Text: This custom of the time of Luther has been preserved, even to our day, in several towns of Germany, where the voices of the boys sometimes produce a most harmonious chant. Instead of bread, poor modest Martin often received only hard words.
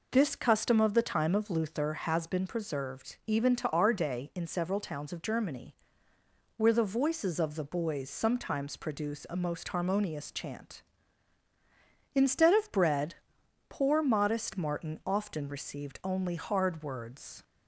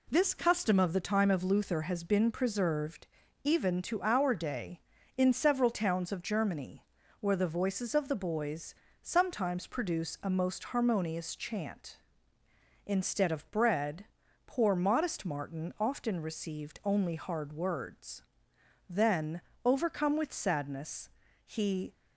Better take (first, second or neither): first